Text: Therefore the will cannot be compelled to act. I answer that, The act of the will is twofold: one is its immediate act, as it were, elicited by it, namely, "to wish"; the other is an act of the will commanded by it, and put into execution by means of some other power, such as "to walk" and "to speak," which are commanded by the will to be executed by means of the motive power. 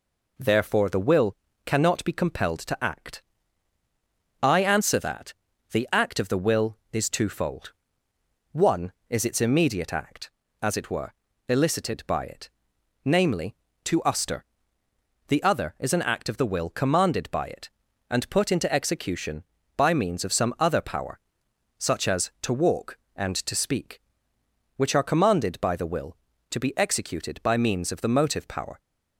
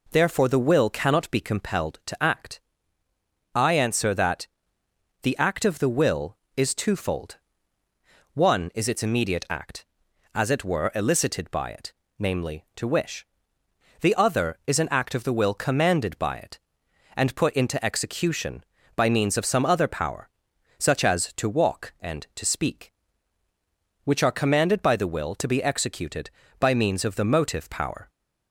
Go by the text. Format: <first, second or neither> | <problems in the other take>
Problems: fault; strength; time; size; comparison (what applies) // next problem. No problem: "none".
second | pauses between "will" and "cannot"; slight; at 1.3 s; 0.28 s long // says "uster" for "wish"; at 14.0 s